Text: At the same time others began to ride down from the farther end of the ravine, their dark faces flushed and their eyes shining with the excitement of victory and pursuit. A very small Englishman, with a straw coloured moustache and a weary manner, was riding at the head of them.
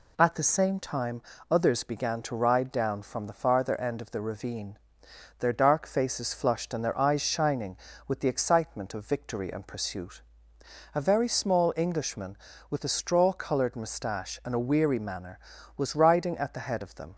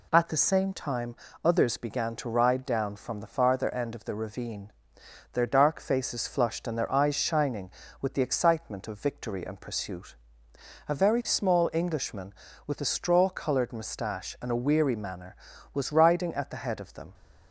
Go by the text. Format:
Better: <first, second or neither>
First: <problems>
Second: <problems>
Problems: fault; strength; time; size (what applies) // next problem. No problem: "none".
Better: neither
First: pauses between "time" and "others"; slight; at 1.2 s; 0.30 s long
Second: pauses between "time" and "others"; slight; at 1.1 s; 0.30 s long